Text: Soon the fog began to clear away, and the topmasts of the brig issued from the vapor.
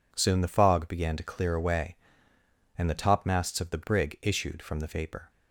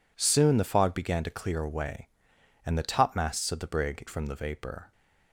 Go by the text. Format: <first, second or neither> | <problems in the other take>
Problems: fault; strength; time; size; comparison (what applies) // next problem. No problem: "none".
first | skips "issued"; at 4.0 s